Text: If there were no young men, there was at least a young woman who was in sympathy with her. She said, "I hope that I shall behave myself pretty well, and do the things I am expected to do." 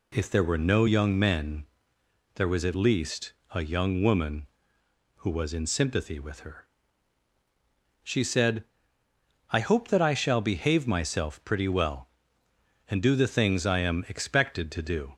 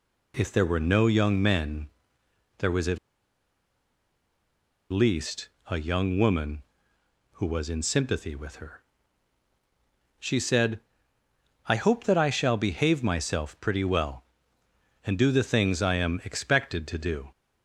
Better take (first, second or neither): first